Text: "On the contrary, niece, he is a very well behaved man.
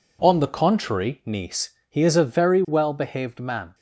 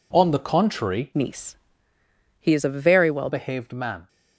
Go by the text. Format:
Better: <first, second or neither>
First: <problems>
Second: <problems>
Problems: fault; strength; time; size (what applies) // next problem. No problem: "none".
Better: first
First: none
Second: changes voice from "niece" to "well"; from 1.1 to 3.2 s; 2.1 s long